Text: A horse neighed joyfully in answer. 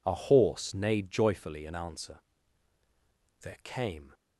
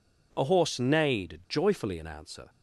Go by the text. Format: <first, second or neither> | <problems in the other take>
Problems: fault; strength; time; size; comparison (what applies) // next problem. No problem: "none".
second | goes on to say "There came"; noticeable; from 3.4 s on; 0.72 s long